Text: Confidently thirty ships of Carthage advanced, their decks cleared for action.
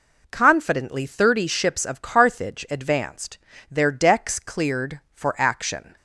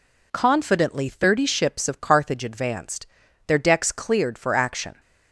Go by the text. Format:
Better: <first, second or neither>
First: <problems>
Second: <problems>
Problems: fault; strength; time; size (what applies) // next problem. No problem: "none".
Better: neither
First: none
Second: none